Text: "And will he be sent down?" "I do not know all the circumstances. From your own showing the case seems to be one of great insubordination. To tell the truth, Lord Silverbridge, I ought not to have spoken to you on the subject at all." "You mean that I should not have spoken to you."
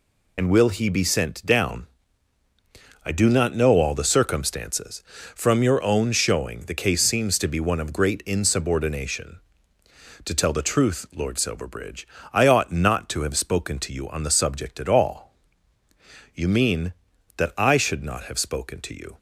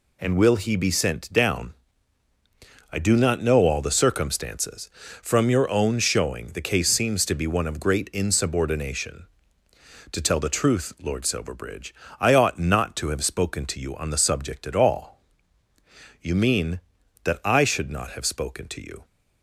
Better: second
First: loses the start of "And"; at 0.3 s; 60 ms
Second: none

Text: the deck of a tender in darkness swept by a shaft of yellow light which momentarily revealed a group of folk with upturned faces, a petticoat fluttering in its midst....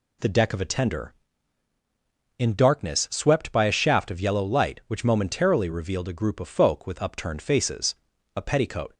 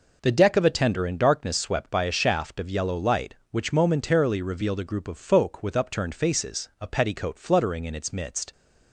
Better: second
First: stops before "fluttering in its midst"; at 8.9 s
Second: none

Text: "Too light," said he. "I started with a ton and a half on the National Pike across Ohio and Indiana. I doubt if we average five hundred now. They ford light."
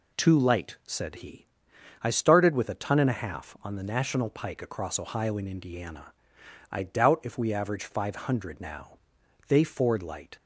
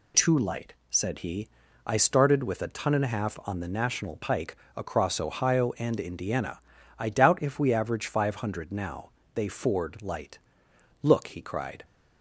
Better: first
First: none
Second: pauses between "Pike" and "across"; slight; at 4.5 s; 0.20 s long // goes on to say "Look he cried"; noticeable; from 11.0 s on; 0.84 s long

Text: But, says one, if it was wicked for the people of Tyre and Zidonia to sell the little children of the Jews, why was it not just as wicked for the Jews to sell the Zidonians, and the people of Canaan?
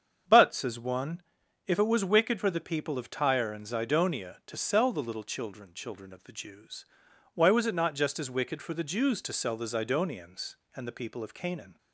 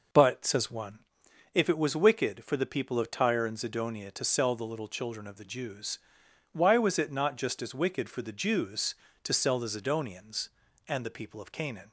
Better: second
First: starts louder than the rest; strong; until 1.7 s; 7.5 dB // says "children" twice; at 5.7 s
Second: none

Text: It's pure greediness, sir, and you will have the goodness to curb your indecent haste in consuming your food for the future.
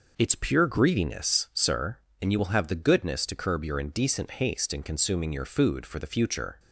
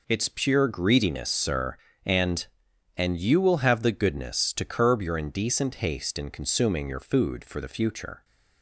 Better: first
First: none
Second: says "and" twice; at 2.9 s

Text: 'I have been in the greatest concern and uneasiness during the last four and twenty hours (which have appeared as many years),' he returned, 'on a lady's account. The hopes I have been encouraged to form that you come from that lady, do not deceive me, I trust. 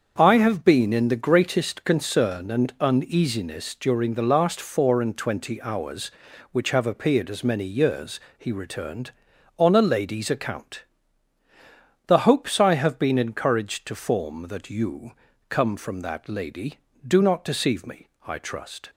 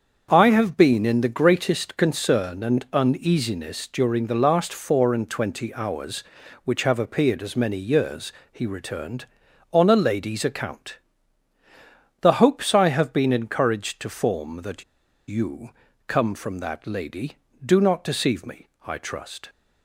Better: first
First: starts louder than the rest; until 1.1 s; 7 dB // pauses between "you" and "come"; at 15.1 s; 0.38 s long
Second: starts louder than the rest; until 1.3 s; 7 dB // pauses between "that" and "you"; at 14.8 s; 0.44 s long // pauses between "you" and "come"; at 15.6 s; 0.38 s long

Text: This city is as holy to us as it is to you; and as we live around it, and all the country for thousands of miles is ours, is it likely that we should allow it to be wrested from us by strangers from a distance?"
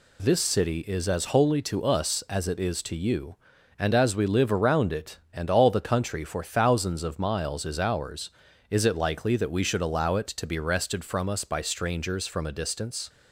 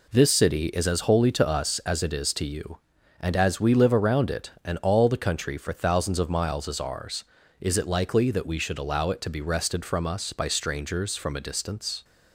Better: neither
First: none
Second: none

